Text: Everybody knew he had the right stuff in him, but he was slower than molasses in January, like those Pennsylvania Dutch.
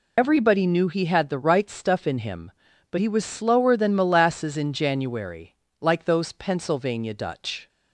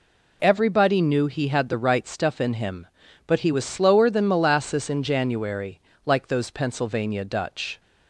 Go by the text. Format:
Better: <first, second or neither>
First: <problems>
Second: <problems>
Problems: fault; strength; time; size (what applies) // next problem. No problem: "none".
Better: second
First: loses the start of "Everybody"; at 0.1 s; 35 ms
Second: none